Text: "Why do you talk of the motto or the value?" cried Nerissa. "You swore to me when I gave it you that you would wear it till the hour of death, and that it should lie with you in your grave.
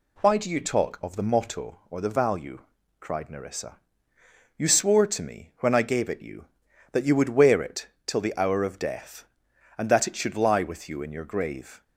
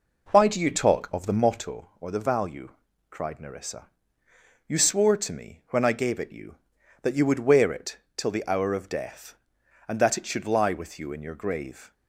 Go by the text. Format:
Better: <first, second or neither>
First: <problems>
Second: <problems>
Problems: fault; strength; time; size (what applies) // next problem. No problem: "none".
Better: first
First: pauses between "it" and "till"; slight; at 7.8 s; 0.18 s long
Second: starts louder than the rest; noticeable; until 1.6 s; 4.5 dB // pauses between "it" and "till"; slight; at 7.9 s; 0.18 s long